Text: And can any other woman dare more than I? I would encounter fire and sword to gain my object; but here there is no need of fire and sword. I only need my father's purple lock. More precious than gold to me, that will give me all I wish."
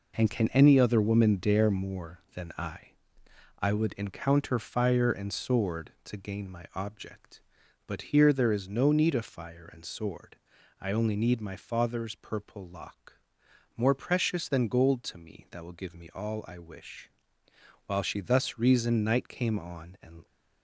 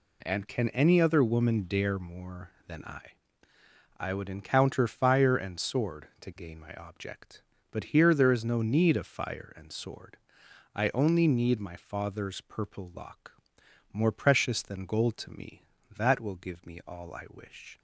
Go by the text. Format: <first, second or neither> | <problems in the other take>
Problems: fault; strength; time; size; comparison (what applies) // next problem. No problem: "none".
second | goes on to say "While she thus reasoned night came on and"; strong; from 17.8 s on; 2.3 s long